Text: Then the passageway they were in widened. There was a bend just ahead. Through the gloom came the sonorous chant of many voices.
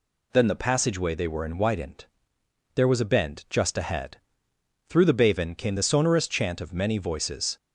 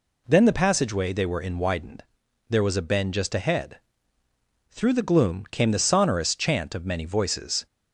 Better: second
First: says "baven" for "gloom"; at 5.3 s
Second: none

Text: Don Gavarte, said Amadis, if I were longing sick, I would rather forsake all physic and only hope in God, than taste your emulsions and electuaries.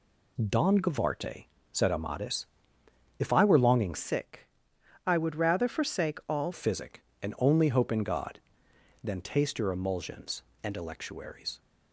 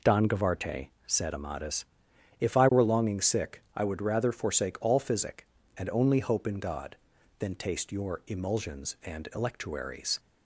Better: second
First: changes voice from "sick" to "all"; from 3.9 to 6.5 s; 2.6 s long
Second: none

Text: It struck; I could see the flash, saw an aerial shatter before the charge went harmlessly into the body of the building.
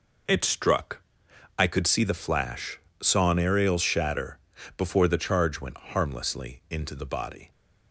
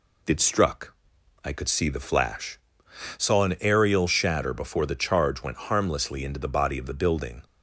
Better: second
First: pauses between "shatter" and "before"; at 4.3 s; 0.38 s long // stops before "of the building"; at 7.5 s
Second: none

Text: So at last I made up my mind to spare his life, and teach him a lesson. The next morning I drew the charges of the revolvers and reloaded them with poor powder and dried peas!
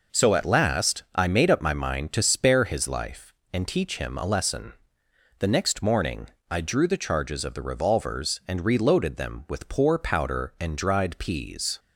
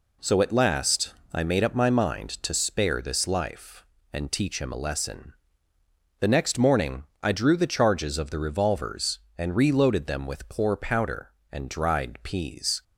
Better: first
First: pauses between "morning" and "I"; slight; at 6.2 s; 0.22 s long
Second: pauses between "last" and "I"; slight; at 1.1 s; 0.20 s long // says "this" for "his"; at 3.0 s // pauses between "morning" and "I"; slight; at 7.0 s; 0.18 s long

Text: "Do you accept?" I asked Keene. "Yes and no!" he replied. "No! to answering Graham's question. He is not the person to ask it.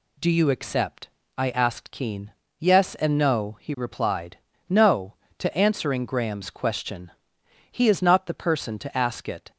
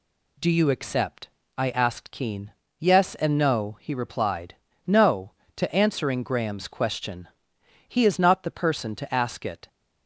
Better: neither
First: none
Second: none

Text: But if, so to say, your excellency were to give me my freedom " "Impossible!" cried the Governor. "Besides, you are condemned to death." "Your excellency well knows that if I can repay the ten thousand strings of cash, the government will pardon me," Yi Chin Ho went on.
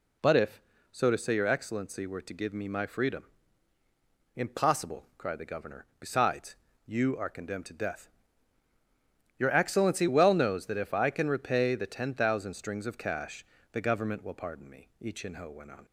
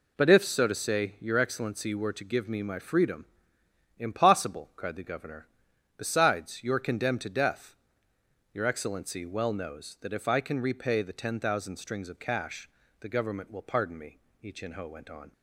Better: neither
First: none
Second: none

